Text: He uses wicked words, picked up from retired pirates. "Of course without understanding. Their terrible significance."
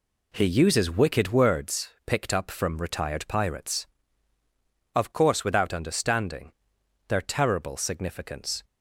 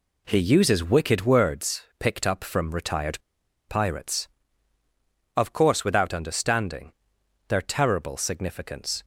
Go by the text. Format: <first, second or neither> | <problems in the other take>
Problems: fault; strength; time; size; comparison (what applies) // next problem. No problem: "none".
first | pauses between "retired" and "pirates"; noticeable; at 3.1 s; 0.49 s long